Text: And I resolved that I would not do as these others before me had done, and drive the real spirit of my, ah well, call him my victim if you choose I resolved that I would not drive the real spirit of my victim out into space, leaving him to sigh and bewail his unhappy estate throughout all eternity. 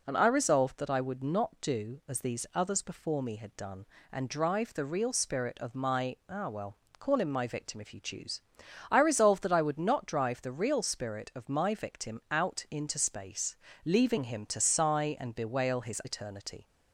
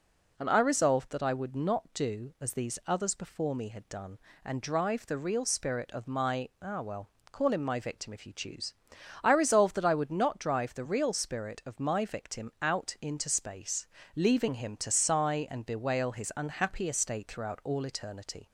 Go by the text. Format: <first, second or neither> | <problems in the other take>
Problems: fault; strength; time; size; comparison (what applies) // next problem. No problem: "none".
second | pauses between "choose" and "I"; noticeable; at 8.3 s; 0.50 s long; noticeable in the second // skips "unhappy estate throughout all"; at 16.0 s